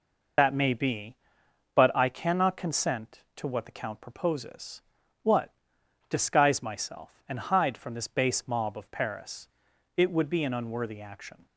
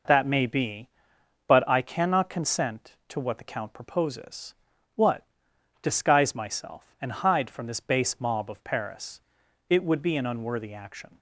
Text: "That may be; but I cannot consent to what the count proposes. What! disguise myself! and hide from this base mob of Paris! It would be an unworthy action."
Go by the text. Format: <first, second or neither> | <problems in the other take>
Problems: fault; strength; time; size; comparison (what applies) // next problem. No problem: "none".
second | loses the start of "That"; at 0.3 s; 55 ms